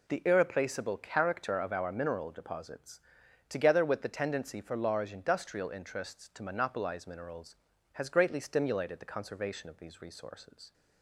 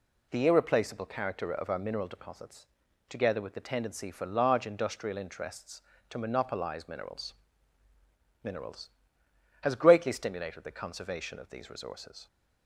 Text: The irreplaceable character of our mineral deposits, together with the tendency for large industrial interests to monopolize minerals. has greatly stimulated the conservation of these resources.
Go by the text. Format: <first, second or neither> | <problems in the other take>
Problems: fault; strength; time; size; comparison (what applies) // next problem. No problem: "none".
first | says "minerals" twice; at 8.4 s